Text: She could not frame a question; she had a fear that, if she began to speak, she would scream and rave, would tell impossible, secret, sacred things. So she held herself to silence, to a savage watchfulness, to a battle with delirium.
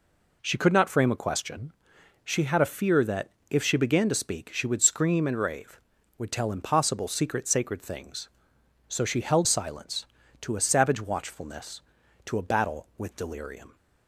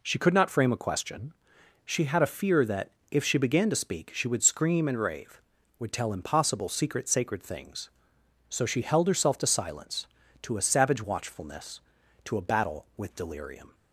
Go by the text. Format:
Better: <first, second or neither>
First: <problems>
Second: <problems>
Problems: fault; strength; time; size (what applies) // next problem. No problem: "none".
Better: second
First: skips "herself to"; at 9.4 s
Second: none